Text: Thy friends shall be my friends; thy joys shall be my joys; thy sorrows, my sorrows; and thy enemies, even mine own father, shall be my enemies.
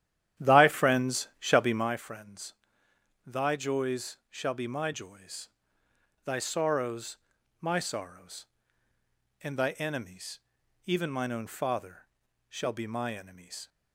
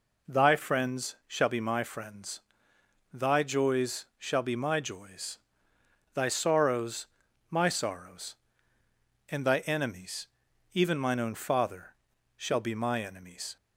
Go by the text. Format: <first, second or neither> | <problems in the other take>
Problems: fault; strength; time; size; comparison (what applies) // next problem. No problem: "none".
second | starts louder than the rest; strong; until 2.0 s; 11 dB